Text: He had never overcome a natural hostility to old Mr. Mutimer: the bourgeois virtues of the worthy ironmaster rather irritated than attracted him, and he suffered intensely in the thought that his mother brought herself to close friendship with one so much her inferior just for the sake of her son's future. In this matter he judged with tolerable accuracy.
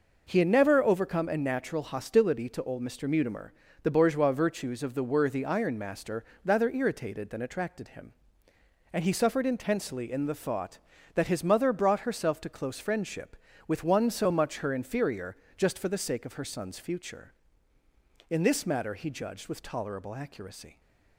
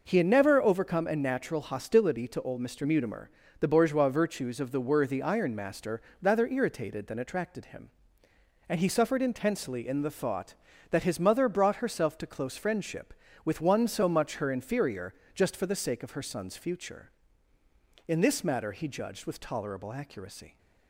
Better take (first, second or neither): neither